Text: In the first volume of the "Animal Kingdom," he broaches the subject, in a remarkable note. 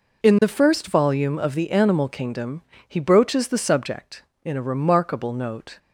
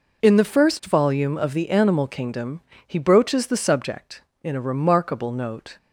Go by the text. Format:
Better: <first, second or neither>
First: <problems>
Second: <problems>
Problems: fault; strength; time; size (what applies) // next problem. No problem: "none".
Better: neither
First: none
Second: none